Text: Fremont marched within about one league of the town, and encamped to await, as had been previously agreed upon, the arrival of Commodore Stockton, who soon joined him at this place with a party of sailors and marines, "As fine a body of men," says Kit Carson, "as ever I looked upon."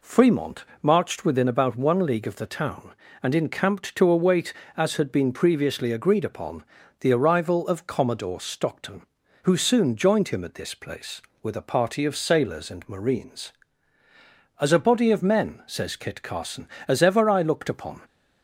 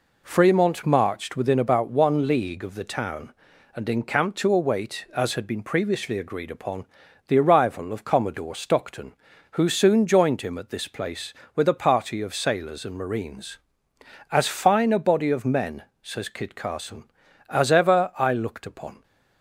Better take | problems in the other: second | pauses between "Fremont" and "marched"; slight; at 0.6 s; 0.18 s long // skips "fine"; at 14.7 s

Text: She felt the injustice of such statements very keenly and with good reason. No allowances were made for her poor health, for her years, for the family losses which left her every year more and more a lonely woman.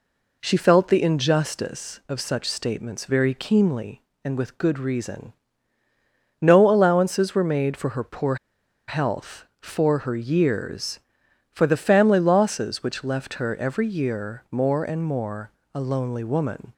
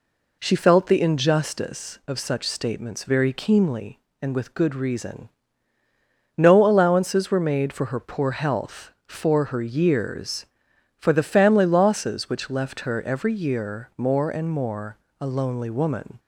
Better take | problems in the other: second | pauses between "poor" and "health"; noticeable; at 8.3 s; 0.52 s long // pauses between "more" and "a"; slight; at 15.5 s; 0.22 s long; slight in the second

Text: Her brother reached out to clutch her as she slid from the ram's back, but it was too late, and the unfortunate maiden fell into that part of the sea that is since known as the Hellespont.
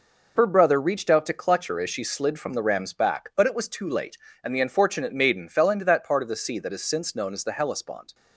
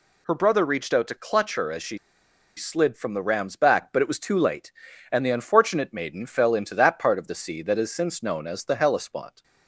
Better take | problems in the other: first | pauses between "she" and "slid"; noticeable; at 1.9 s; 0.59 s long

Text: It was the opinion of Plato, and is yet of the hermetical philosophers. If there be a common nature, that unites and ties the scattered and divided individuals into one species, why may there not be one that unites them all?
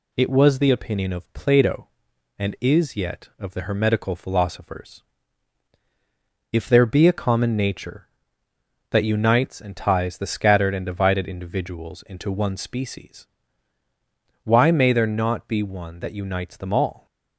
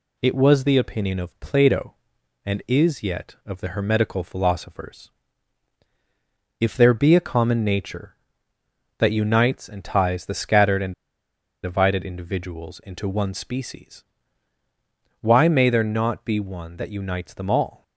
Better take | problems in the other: first | pauses between "and" and "divided"; noticeable; at 10.9 s; 0.71 s long

